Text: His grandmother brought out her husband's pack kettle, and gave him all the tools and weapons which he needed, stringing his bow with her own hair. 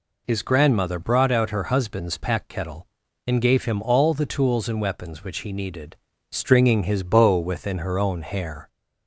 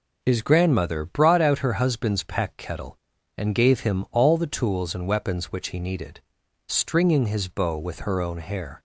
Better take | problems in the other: second | says "within" for "with"; at 7.3 s

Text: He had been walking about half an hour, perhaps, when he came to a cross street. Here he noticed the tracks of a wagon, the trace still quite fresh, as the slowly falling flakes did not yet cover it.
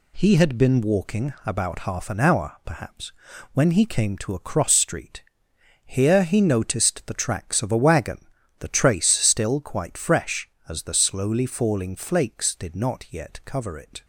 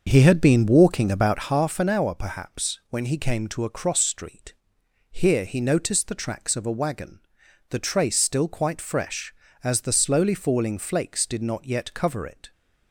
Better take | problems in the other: first | starts louder than the rest; until 1.6 s; 6 dB

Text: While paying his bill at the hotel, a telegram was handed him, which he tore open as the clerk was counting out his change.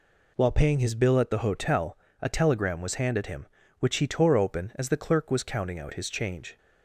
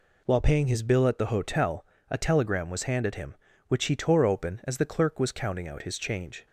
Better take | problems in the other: neither | none

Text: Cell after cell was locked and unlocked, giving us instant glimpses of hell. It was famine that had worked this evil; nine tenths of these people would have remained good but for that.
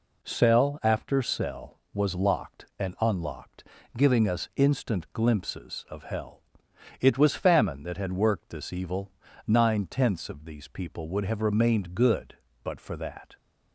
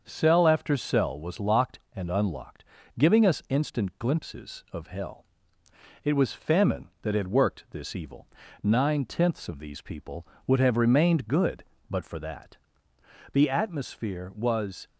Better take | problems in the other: first | starts louder than the rest; until 1.0 s; 6.5 dB // goes on to say "The atmosphere was"; from 13.3 s on; 1.5 s long

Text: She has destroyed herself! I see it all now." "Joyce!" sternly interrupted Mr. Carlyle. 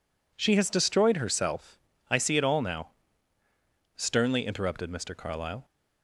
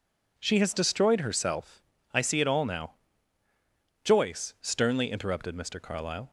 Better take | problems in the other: second | skips "Joyce"; at 3.4 s

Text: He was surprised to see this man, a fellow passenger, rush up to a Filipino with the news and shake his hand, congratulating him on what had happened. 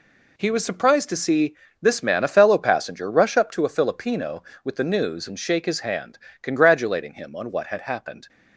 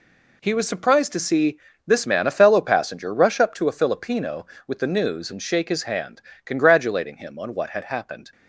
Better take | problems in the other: neither | pauses between "see" and "this"; slight; the same in both

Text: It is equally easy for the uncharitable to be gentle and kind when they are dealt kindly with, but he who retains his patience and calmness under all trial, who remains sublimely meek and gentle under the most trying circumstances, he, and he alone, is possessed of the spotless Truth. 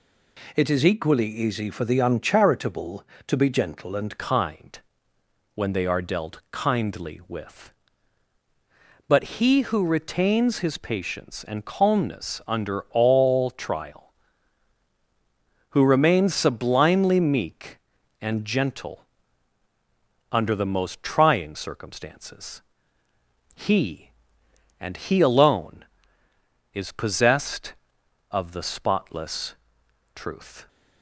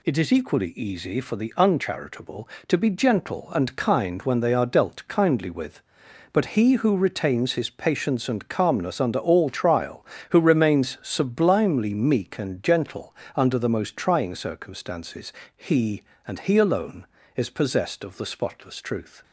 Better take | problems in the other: second | changes voice at "kind"; from 4.1 s on; 26.5 s long // pauses between "kind" and "when"; noticeable; at 4.7 s; 0.74 s long // pauses between "gentle" and "under"; at 19.0 s; 1.2 s long; slight in the second // pauses between "spotless" and "Truth"; noticeable; at 29.5 s; 0.60 s long

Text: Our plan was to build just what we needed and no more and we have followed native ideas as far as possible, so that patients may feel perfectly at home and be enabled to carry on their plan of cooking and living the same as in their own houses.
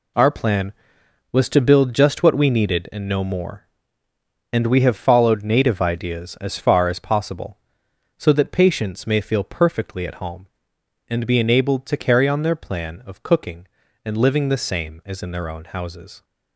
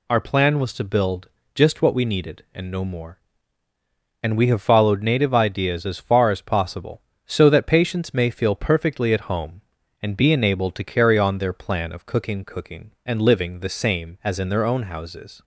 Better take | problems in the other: first | pauses between "build" and "just"; slight; at 1.2 s; 0.26 s long // says "cooking" twice; at 12.4 s

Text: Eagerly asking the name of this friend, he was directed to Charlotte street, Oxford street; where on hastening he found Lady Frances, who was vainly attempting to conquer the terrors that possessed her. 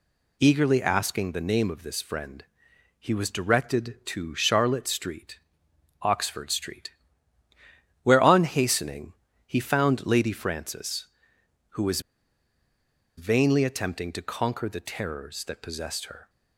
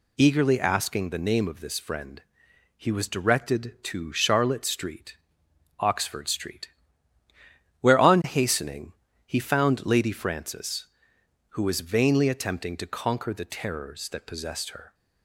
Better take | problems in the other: second | pauses between "hastening" and "he"; slight; at 9.1 s; 0.34 s long; slight in the second // pauses between "was" and "vainly"; at 12.0 s; 1.1 s long

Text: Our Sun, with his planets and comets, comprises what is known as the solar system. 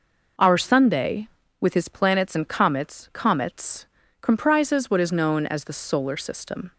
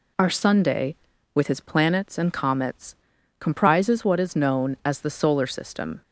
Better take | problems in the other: second | says "comets" twice; at 3.1 s

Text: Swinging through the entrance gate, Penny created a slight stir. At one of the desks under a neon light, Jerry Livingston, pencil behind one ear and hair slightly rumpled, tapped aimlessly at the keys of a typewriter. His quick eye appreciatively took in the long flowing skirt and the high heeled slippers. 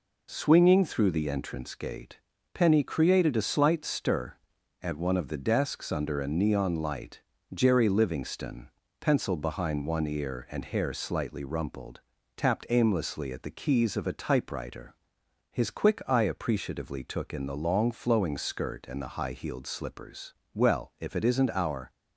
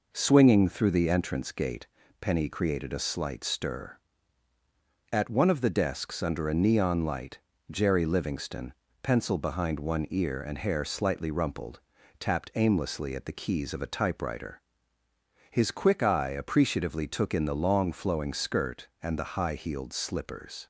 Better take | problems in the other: second | goes on to say "Well if it isn't our"; from 20.5 s on; 1.3 s long

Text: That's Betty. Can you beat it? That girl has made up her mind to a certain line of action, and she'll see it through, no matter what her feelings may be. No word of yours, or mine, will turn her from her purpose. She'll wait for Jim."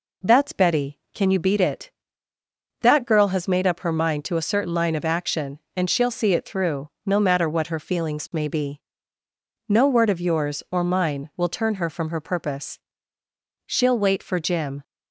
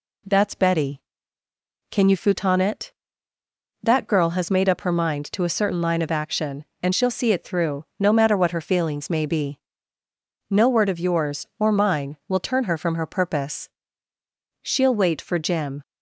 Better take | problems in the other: first | says "futon" for "beat"; at 2.1 s

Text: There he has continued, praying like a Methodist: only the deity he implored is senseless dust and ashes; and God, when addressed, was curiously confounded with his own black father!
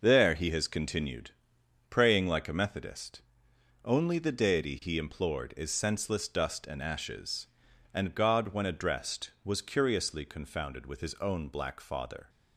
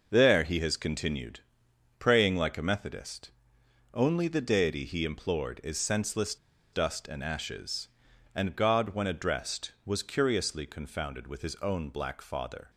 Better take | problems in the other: first | pauses between "senseless" and "dust"; at 6.3 s; 0.37 s long

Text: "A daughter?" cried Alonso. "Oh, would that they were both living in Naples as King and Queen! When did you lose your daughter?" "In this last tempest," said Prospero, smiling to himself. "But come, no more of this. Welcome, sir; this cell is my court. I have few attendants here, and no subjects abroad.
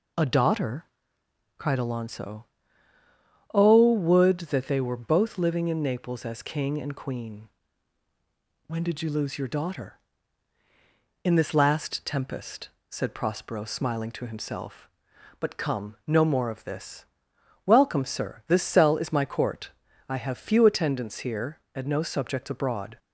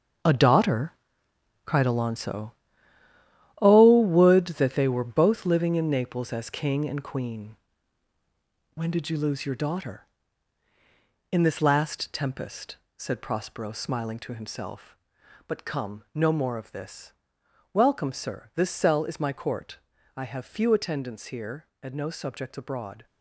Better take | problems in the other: first | gets quieter; strong; throughout; 11 dB

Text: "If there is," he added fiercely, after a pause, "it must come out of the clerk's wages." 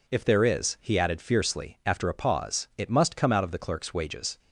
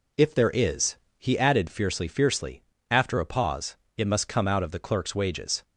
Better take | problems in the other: first | says "fiercely" twice; at 2.0 s

